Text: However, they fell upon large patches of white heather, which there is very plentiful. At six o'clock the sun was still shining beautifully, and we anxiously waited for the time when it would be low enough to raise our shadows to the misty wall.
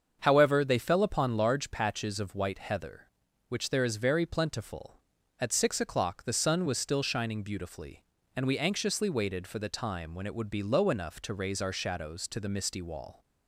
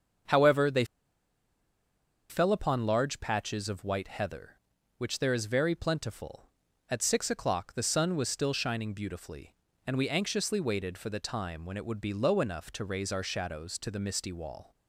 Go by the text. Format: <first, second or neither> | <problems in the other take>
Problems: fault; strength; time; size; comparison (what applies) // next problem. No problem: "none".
first | starts louder than the rest; until 2.7 s; 7 dB; also in the first // pauses between "they" and "fell"; strong; at 0.8 s; 1.4 s long